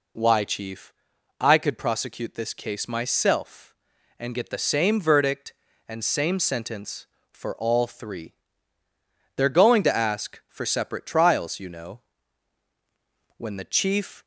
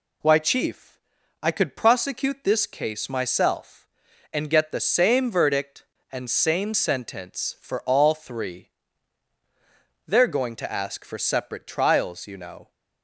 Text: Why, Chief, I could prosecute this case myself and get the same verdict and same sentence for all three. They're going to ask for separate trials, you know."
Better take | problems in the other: second | goes on to say "When the Chief"; noticeable; from 13.3 s on; 0.88 s long

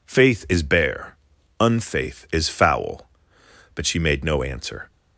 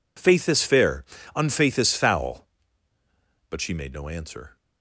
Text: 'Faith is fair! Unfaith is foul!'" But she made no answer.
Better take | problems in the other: second | says "bare" for "fair"; at 0.6 s

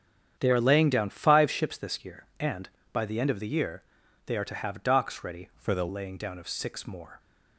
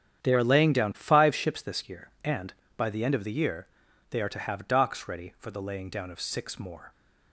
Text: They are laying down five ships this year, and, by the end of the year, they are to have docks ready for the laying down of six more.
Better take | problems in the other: second | starts louder than the rest; strong; until 1.3 s; 8.5 dB; strong in the second // changes voice from "for" to "the"; from 5.5 to 5.8 s; 0.3 s long

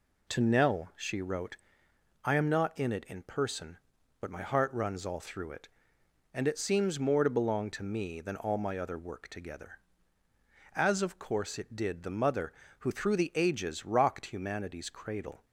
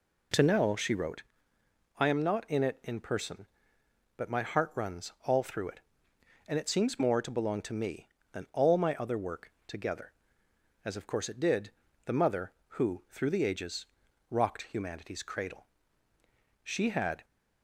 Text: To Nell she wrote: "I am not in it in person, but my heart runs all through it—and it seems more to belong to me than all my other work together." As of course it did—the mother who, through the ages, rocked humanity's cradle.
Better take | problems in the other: first | goes on to say "She had"; noticeable; from 16.6 s on; 0.62 s long

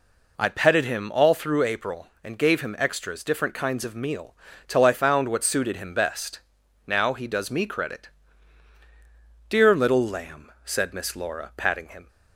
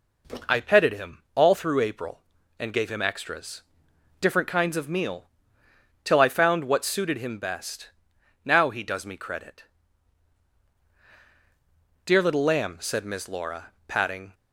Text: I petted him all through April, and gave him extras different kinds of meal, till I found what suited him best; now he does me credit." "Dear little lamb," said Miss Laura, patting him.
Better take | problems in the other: first | pauses between "extras" and "different"; noticeable; at 3.6 s; 0.60 s long // stops before "him"; at 14.3 s

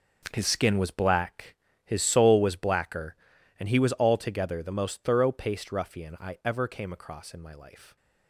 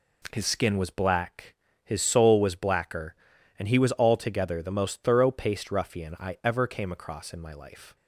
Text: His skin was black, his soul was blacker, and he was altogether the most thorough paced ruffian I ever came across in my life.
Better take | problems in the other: second | gets quieter; strong; throughout; 12.5 dB

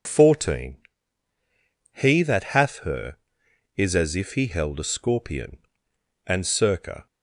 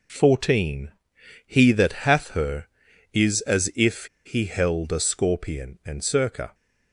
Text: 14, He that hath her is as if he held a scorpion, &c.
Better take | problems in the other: first | pauses between "if" and "he"; slight; at 4.0 s; 0.18 s long

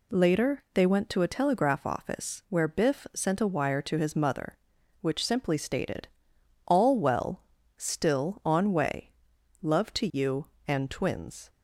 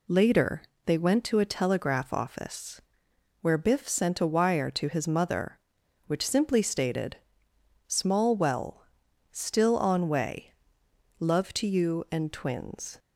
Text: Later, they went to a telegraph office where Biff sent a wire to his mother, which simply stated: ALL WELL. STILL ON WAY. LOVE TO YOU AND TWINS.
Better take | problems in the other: first | pauses between "office" and "where"; noticeable; at 2.8 s; 0.60 s long // says "Small" for "ALL"; at 7.8 s

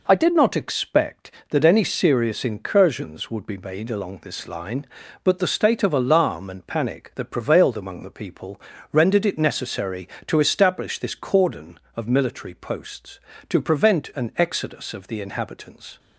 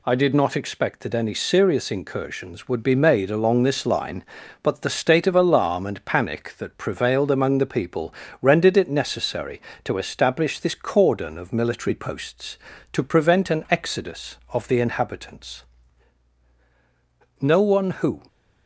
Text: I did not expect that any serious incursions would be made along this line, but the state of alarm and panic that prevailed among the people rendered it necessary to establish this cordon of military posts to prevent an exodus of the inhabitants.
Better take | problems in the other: first | pauses between "people" and "rendered"; slight; at 8.1 s; 0.28 s long; slight in the first // goes on to say "No one who"; noticeable; from 17.4 s on; 0.80 s long

